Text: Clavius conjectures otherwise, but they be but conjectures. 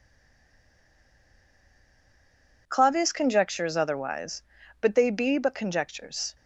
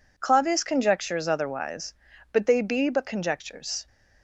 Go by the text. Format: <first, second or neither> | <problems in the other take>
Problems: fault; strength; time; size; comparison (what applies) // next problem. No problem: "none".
second | stays silent before the first word; strong; until 2.6 s; 2.6 s long